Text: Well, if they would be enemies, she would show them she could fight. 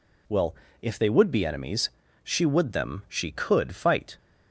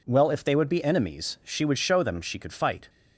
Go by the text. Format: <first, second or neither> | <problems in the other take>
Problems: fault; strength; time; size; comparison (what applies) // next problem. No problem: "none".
second | skips "show"; at 2.7 s